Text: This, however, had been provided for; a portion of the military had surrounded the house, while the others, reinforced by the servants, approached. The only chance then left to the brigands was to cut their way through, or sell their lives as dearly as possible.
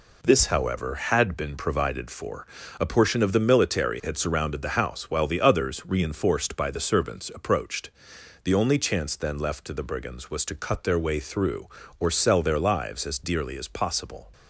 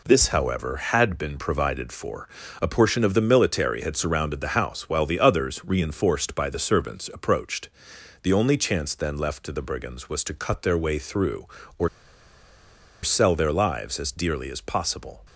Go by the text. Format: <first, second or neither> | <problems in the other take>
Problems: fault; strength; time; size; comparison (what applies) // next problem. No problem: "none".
first | pauses between "or" and "sell"; at 11.8 s; 1.1 s long